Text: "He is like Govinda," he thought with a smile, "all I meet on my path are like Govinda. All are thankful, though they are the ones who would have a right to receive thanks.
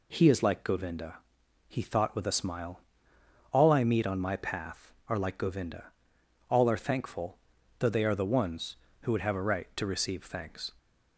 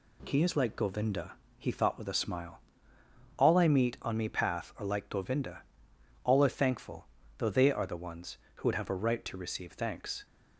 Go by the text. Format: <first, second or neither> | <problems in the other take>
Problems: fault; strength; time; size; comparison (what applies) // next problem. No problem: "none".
first | says "me" for "my"; at 4.1 s